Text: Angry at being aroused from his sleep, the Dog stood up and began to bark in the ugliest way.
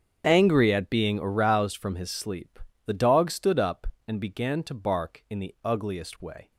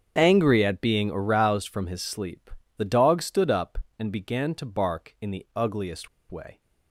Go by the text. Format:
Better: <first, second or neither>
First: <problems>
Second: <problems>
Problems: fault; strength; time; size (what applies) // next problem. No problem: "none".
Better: first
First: starts louder than the rest; strong; until 1.2 s; 7.5 dB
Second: starts louder than the rest; strong; until 1.1 s; 8 dB // pauses between "ugliest" and "way"; slight; at 6.0 s; 0.21 s long